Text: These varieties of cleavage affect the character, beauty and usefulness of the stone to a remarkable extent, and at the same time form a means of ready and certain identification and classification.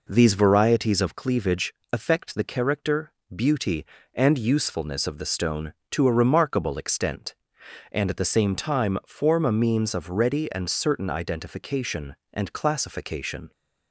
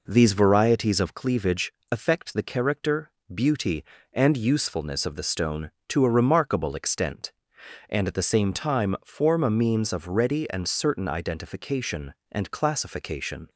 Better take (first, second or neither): neither